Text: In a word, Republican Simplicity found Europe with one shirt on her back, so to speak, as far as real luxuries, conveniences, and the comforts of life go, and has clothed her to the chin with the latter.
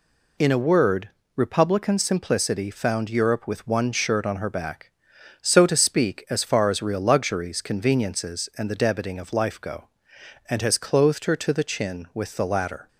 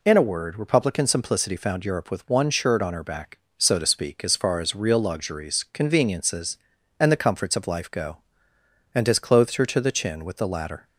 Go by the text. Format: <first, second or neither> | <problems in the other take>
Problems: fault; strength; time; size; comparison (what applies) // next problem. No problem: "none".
second | says "debiting" for "comforts"; at 8.7 s